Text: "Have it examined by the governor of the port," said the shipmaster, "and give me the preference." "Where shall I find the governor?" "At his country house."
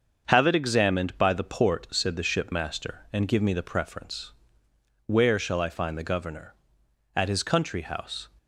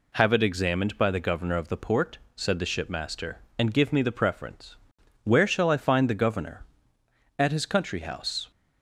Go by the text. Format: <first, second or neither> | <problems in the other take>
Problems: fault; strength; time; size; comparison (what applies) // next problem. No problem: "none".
second | starts louder than the rest; until 1.3 s; 7 dB // skips "the governor of"; at 1.3 s